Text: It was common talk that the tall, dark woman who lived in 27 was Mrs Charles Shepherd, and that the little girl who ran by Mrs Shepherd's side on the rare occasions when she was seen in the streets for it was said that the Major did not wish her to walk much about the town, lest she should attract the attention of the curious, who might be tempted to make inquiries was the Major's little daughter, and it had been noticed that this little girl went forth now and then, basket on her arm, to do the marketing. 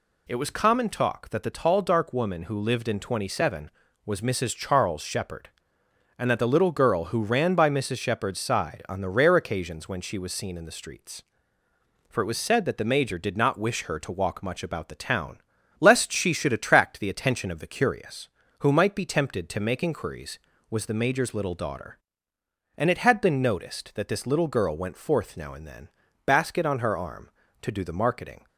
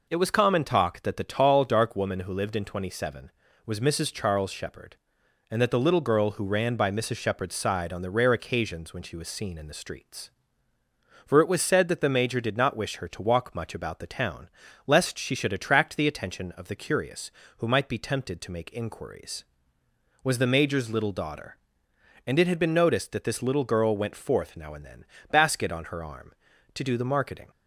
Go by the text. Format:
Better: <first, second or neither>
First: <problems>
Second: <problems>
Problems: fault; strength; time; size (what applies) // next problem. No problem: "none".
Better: neither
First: none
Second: none